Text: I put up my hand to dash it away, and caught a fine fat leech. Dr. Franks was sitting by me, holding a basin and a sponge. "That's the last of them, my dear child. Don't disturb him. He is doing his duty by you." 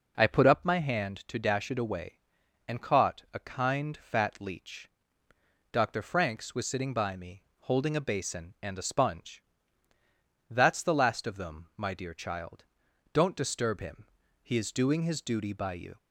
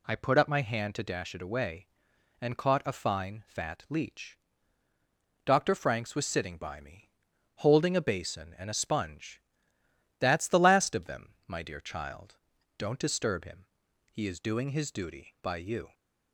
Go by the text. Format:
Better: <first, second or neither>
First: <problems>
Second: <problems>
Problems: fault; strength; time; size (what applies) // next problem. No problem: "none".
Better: second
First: says "kind" for "fine"; at 3.3 s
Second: none